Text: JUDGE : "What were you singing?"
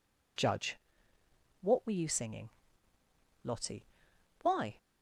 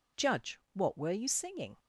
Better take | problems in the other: second | goes on to say "LOTTIE Why"; from 3.4 s on; 1.3 s long

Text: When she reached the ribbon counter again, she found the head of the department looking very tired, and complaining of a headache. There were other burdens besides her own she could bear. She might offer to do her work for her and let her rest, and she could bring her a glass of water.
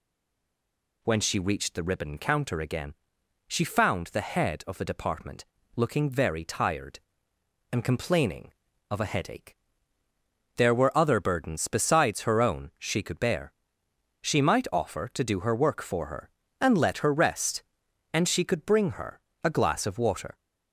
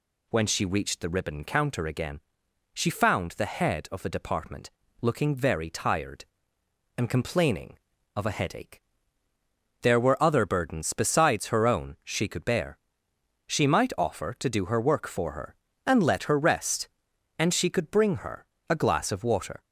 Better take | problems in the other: second | stays silent before the first word; until 1.0 s; 1.0 s long // pauses between "department" and "looking"; slight; at 5.4 s; 0.30 s long; slight in the second // pauses between "her" and "a"; slight; at 19.2 s; 0.24 s long; slight in the second

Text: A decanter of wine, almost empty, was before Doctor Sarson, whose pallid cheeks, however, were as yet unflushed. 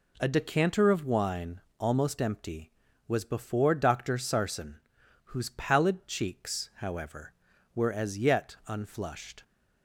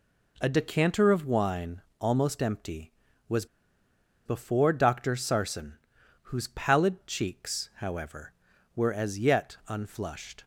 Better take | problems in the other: first | pauses between "was" and "before"; noticeable; at 3.4 s; 0.79 s long

